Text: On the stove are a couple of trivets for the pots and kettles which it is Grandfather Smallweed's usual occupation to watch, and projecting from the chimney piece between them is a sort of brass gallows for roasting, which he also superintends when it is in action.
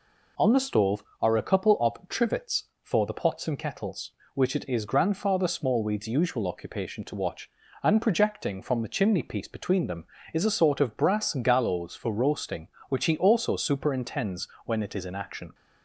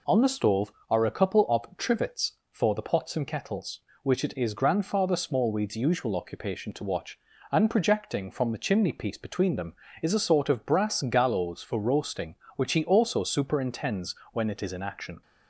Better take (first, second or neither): neither